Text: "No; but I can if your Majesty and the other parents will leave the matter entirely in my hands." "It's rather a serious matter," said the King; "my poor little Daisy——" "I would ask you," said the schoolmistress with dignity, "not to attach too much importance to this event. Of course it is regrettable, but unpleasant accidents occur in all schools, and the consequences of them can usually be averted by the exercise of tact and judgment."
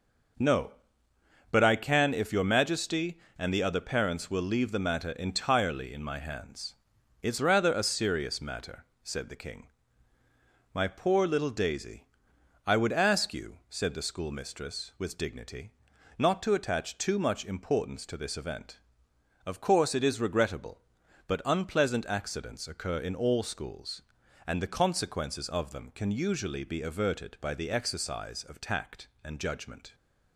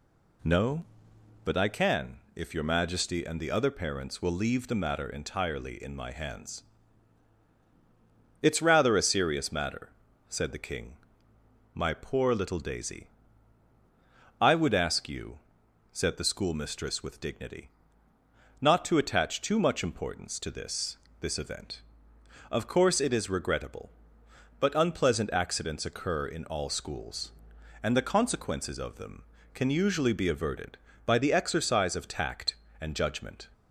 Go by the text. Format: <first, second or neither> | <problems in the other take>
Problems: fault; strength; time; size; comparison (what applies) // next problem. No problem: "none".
first | pauses between "can" and "if"; slight; at 2.1 s; 0.16 s long // says "this" twice; at 21.2 s